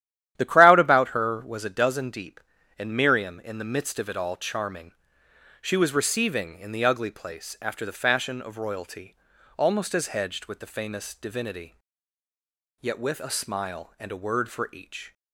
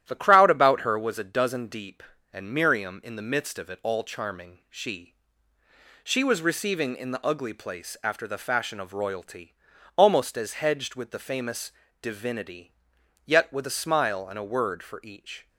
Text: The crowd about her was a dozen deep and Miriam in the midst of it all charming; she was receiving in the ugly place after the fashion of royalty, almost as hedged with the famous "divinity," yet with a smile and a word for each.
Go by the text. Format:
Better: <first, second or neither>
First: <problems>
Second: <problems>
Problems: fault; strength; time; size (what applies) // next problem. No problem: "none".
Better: first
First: starts louder than the rest; strong; until 1.3 s; 11.5 dB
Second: starts louder than the rest; strong; until 1.0 s; 12 dB // says "she" twice; at 6.0 s // pauses between "famous" and "divinity"; slight; at 11.7 s; 0.30 s long